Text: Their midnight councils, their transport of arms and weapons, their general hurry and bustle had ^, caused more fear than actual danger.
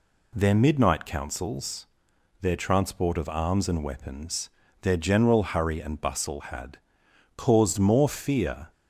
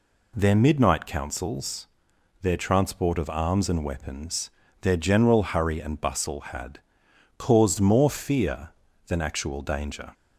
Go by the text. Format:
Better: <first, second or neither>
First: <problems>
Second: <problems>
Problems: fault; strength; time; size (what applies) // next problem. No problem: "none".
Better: second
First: stops before "than actual danger"; at 8.7 s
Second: none